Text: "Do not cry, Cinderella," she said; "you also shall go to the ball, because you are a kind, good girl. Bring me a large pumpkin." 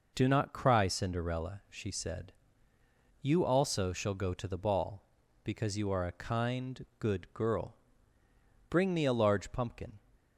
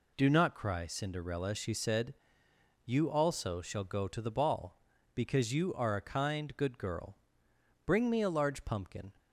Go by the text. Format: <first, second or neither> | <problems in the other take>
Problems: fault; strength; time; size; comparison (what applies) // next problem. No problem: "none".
neither | none